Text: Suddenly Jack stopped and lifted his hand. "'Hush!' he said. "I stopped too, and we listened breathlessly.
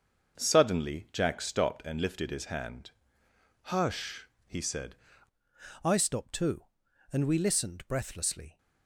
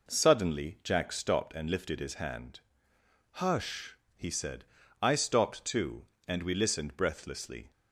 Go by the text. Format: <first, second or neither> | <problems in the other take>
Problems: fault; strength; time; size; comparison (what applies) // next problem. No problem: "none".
second | starts louder than the rest; until 1.4 s; 6.5 dB // changes voice at "I"; from 5.8 s on; 2.7 s long